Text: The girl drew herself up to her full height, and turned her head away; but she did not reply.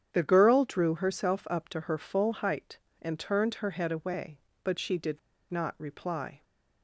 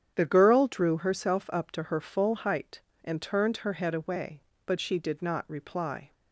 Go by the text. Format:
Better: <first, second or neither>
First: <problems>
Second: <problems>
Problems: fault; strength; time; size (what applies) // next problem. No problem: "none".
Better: second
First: starts louder than the rest; strong; until 1.1 s; 8.5 dB // pauses between "did" and "not"; slight; at 5.1 s; 0.31 s long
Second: starts louder than the rest; strong; until 1.1 s; 8.5 dB